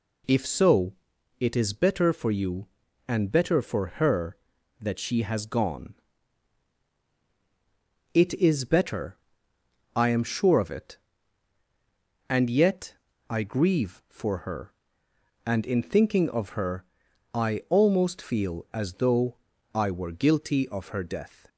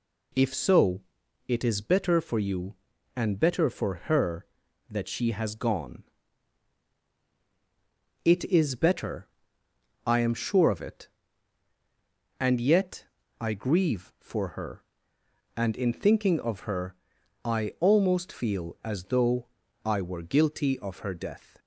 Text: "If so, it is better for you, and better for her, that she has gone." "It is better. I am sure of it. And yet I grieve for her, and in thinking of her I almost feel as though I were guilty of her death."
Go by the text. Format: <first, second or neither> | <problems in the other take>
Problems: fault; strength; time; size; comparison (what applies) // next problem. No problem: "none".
neither | pauses between "yet" and "I"; slight; the same in both // pauses between "her" and "I"; noticeable; the same in both // pauses between "though" and "I"; the same in both